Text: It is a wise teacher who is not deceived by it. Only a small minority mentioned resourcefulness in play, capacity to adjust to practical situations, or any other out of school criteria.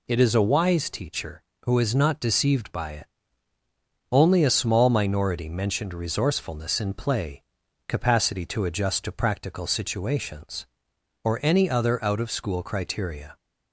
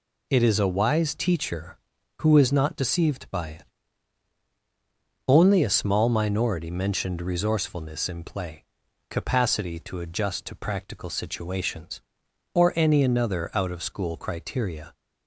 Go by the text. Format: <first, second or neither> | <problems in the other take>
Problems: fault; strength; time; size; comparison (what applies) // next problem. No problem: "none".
first | says "another" for "other"; at 13.0 s